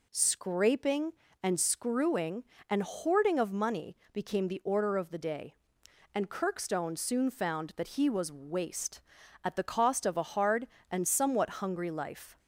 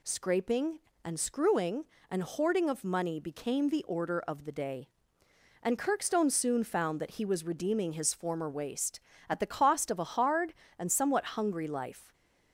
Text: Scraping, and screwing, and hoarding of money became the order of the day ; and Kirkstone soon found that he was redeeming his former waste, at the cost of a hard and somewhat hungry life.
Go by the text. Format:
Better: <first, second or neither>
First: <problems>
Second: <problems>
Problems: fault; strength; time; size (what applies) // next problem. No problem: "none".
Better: second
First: pauses between "money" and "became"; slight; at 3.9 s; 0.16 s long // skips "redeeming his former"; at 8.3 s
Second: none